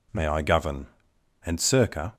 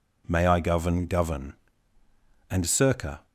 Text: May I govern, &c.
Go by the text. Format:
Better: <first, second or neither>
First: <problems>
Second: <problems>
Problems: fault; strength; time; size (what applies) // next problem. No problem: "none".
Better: first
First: none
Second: says "govern" twice; at 1.0 s